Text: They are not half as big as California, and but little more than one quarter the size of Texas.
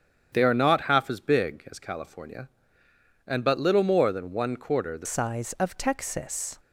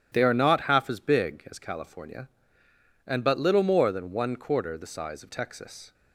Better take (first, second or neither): second